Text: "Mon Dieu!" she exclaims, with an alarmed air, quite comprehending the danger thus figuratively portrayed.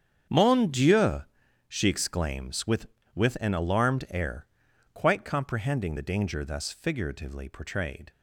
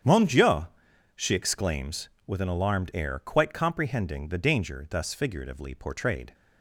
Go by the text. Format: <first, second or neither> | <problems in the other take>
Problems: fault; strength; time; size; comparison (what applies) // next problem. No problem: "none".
second | starts louder than the rest; strong; until 1.7 s; 8 dB; strong in the second // says "with" twice; at 3.1 s